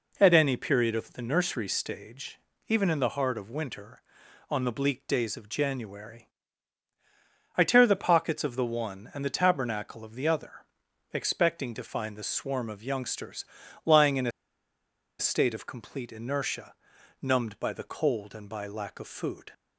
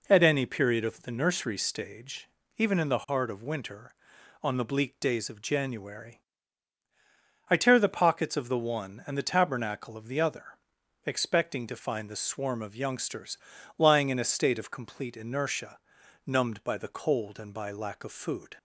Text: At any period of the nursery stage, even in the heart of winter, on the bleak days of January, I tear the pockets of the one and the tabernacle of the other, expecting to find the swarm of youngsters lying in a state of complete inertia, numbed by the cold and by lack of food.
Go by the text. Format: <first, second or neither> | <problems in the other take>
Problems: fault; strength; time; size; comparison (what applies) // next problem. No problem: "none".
second | pauses between "youngsters" and "lying"; at 13.4 s; 0.40 s long; also in the second // pauses between "a" and "state"; noticeable; at 14.3 s; 0.88 s long